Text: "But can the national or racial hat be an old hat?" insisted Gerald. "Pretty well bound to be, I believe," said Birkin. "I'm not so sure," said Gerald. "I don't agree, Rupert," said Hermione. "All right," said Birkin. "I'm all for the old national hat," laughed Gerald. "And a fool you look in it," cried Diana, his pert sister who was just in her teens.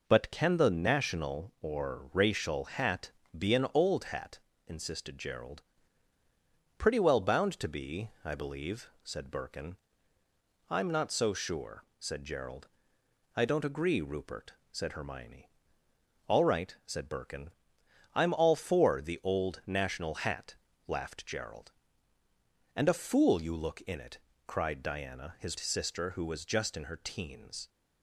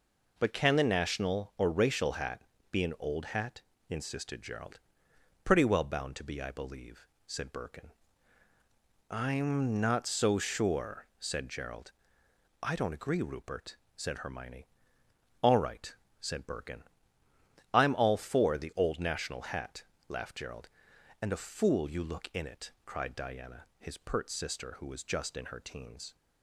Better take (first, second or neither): second